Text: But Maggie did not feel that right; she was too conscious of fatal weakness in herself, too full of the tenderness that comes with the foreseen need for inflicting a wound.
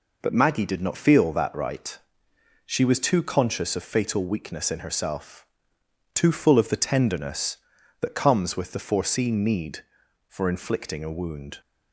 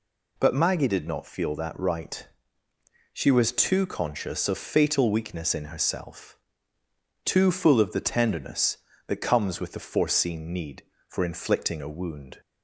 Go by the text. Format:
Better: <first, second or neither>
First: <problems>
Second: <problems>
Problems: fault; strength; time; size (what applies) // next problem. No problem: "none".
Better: neither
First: none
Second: none